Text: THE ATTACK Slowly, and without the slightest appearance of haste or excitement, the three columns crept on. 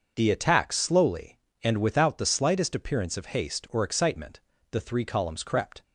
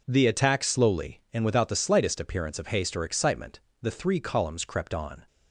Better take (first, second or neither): second